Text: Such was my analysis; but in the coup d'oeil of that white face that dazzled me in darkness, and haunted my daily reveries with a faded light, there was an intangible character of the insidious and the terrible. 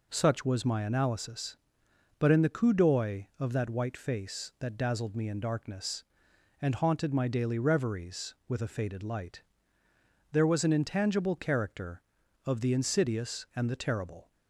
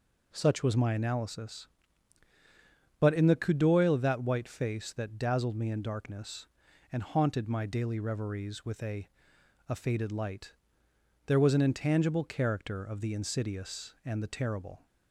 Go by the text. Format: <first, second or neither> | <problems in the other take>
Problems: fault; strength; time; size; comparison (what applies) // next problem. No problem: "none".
first | says "a" twice; at 9.6 s